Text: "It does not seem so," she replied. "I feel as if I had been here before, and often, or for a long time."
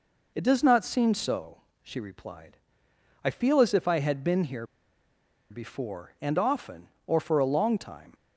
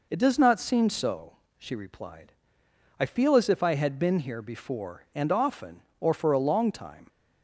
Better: second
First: pauses between "here" and "before"; noticeable; at 4.6 s; 0.85 s long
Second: none

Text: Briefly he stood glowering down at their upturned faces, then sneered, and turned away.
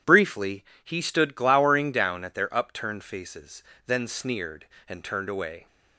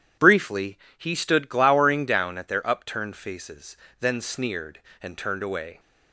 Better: neither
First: pauses between "Briefly" and "he"; slight; at 0.6 s; 0.20 s long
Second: pauses between "Briefly" and "he"; slight; at 0.7 s; 0.20 s long

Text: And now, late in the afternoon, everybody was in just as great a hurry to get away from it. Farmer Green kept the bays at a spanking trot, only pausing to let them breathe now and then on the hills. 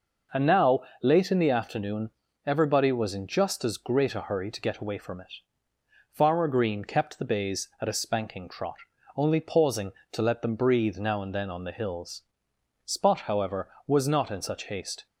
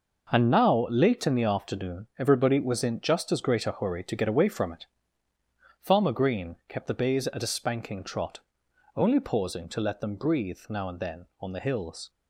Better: second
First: goes on to say "Spot however was not in such haste"; strong; from 12.8 s on; 2.2 s long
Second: none

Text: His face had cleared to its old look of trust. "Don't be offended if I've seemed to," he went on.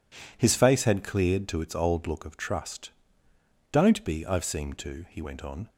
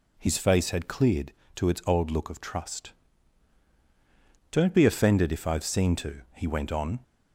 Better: second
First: skips "offended if"; at 4.2 s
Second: none

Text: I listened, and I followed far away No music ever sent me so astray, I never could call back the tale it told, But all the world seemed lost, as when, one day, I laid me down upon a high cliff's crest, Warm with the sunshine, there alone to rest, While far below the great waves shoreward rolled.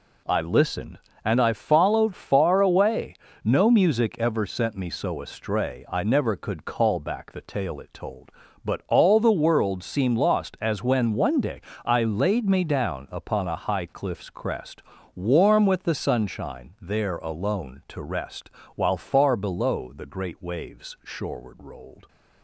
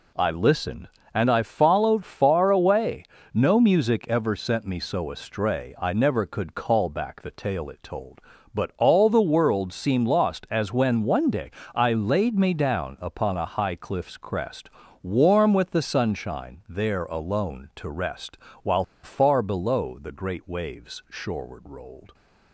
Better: first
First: pauses between "away" and "No"; slight; at 3.1 s; 0.28 s long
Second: pauses between "away" and "No"; slight; at 3.0 s; 0.28 s long // pauses between "While" and "far"; slight; at 18.8 s; 0.20 s long

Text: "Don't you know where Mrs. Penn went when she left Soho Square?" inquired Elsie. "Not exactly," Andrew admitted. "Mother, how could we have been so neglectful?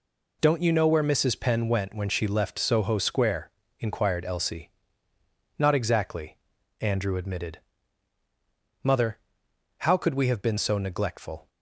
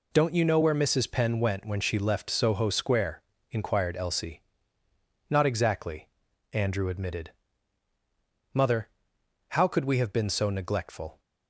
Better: neither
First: none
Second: none

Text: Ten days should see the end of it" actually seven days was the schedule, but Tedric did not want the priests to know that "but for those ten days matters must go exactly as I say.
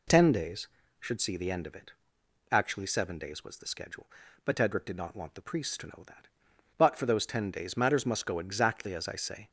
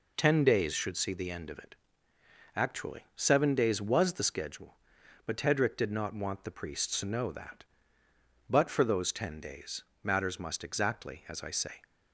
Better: first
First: pauses between "it" and "actually"; noticeable; at 1.9 s; 0.58 s long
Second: pauses between "it" and "actually"; noticeable; at 1.7 s; 0.80 s long // pauses between "days" and "matters"; slight; at 9.8 s; 0.18 s long // skips "go"; at 10.6 s

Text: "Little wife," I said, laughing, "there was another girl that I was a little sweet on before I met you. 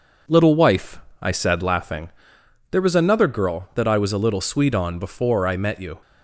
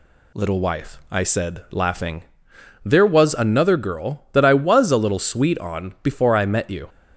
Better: neither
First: none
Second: none

